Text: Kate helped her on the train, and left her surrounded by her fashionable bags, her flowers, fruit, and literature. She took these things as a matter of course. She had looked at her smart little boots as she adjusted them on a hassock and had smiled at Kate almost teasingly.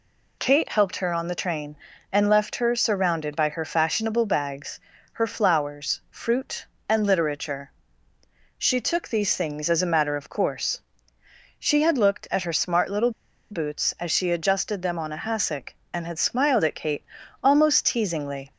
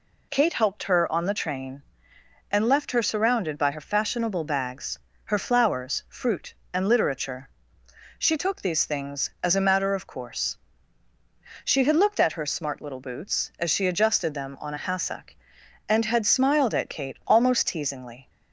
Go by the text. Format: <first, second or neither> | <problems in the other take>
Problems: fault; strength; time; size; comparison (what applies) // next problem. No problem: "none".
second | pauses between "little" and "boots"; at 13.0 s; 0.40 s long // pauses between "Kate" and "almost"; slight; at 17.0 s; 0.36 s long